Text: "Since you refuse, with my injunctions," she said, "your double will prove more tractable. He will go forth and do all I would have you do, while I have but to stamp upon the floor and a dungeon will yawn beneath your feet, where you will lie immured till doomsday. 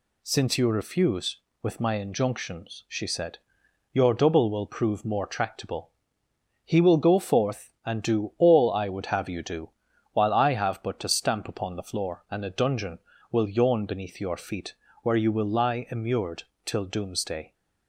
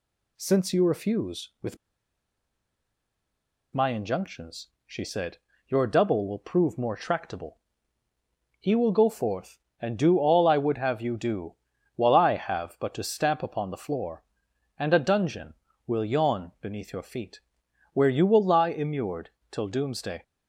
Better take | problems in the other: first | pauses between "with" and "my"; strong; at 1.7 s; 1.9 s long // pauses between "immured" and "till"; slight; at 19.3 s; 0.20 s long; slight in the first

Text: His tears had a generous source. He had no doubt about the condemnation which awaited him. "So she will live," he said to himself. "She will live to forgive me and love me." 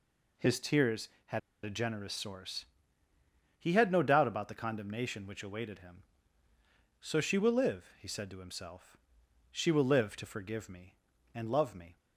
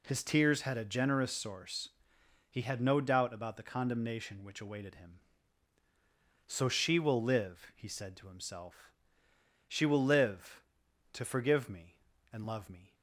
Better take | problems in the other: second | pauses between "had" and "a"; slight; at 1.3 s; 0.24 s long

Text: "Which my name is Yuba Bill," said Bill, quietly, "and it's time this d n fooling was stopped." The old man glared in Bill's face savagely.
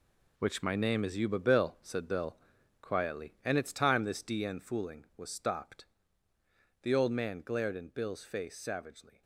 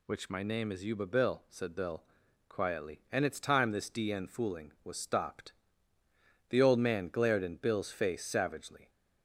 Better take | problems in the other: second | gets quieter; strong; throughout; 10 dB

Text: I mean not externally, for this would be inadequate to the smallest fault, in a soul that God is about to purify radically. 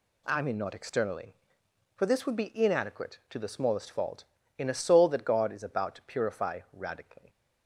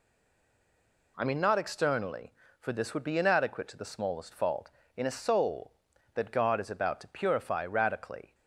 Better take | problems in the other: first | stays silent before the first word; until 1.1 s; 1.1 s long

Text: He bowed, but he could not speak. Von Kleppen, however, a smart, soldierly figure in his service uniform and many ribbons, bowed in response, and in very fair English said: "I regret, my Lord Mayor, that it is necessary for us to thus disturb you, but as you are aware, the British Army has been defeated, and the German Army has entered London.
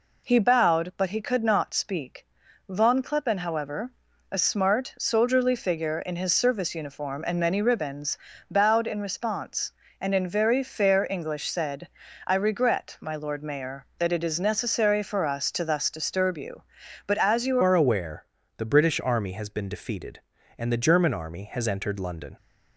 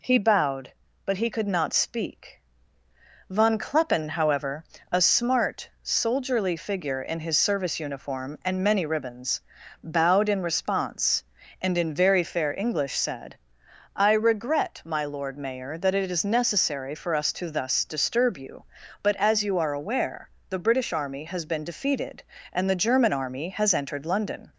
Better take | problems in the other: second | changes voice at "are"; from 17.6 s on; 4.7 s long

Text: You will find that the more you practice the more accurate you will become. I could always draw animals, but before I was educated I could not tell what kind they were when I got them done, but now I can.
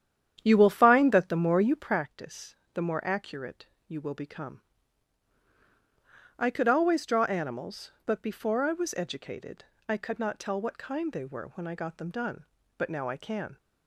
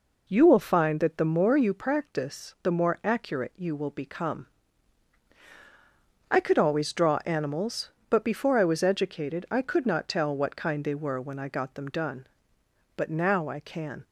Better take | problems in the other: second | starts louder than the rest; strong; until 2.0 s; 9.5 dB // pauses between "practice" and "the"; slight; at 2.5 s; 0.20 s long // pauses between "accurate" and "you"; slight; at 3.6 s; 0.22 s long // pauses between "educated" and "I"; slight; at 9.6 s; 0.24 s long

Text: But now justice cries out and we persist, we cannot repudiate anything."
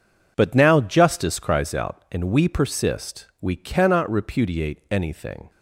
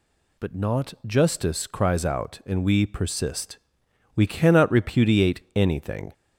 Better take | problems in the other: first | says "not" for "now"; at 0.5 s

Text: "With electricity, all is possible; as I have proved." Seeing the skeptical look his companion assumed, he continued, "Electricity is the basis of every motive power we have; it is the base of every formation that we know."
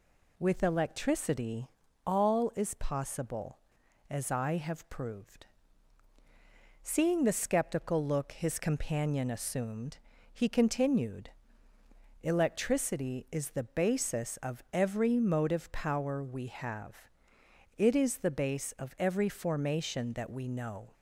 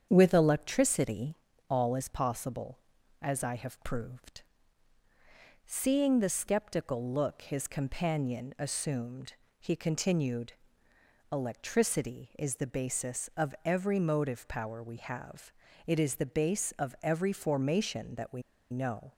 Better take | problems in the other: first | starts louder than the rest; strong; until 1.1 s; 8 dB // pauses between "we" and "know"; slight; at 18.4 s; 0.30 s long

